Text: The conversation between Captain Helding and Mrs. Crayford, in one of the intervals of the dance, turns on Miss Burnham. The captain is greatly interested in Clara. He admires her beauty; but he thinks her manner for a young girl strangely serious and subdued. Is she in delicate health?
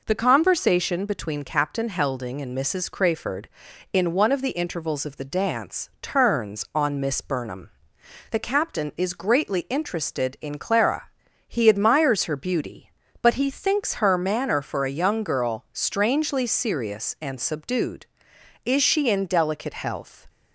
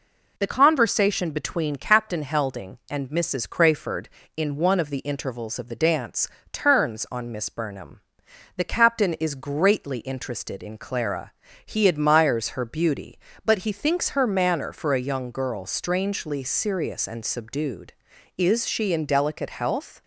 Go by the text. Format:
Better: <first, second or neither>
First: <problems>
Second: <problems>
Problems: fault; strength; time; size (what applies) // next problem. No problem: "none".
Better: neither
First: none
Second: none